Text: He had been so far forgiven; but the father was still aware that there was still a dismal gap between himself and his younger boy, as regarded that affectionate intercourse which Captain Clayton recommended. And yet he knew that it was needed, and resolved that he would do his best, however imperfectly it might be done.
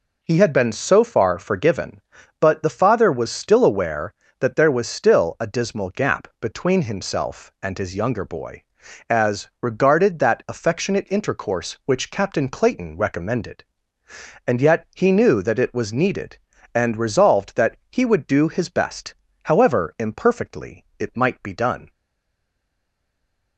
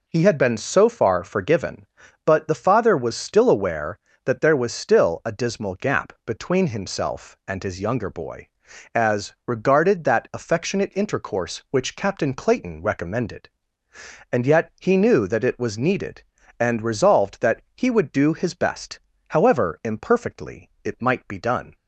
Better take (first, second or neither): second